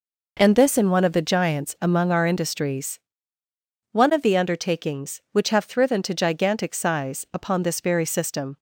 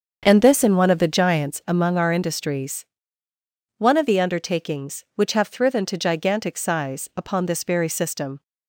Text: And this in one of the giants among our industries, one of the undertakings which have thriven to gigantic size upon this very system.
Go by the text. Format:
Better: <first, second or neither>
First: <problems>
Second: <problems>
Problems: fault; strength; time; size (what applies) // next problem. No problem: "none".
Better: first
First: none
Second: starts louder than the rest; until 1.5 s; 7 dB